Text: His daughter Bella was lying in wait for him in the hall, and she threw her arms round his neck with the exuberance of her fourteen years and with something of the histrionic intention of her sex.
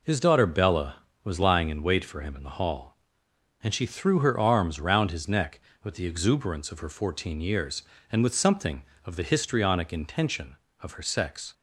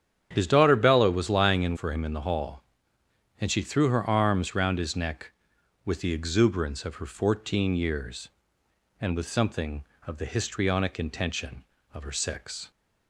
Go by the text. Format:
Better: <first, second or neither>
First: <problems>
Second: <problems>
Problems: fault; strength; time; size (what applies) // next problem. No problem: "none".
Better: first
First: none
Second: starts louder than the rest; strong; until 1.3 s; 9 dB // skips "wait"; at 1.7 s